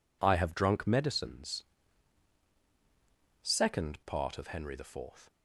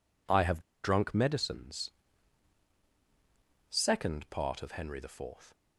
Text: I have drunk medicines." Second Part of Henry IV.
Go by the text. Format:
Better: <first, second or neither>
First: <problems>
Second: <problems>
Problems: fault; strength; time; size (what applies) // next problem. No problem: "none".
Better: first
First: none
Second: pauses between "have" and "drunk"; slight; at 0.6 s; 0.21 s long